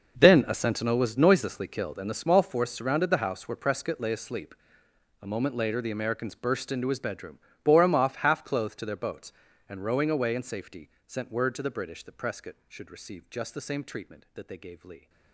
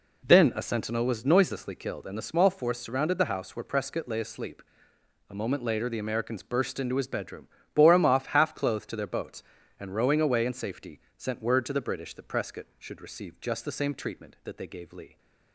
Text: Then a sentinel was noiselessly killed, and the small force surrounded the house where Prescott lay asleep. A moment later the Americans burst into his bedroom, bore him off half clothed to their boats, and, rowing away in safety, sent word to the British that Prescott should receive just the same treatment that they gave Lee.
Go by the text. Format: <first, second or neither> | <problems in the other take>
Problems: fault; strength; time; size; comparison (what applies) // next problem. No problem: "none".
second | gets quieter; strong; throughout; 16 dB